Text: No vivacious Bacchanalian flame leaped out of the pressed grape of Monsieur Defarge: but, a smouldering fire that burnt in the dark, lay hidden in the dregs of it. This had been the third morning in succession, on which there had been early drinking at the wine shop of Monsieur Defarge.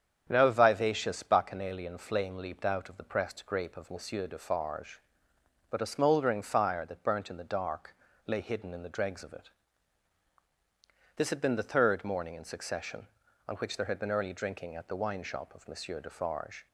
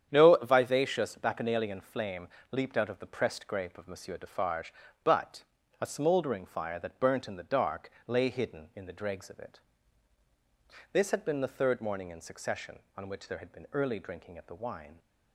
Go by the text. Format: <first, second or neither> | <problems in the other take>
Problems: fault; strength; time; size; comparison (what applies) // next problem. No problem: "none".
first | starts louder than the rest; strong; until 1.1 s; 9 dB; strong in the first // pauses between "flame" and "leaped"; slight; at 2.2 s; 0.22 s long // stops before "shop of Monsieur Defarge"; at 14.9 s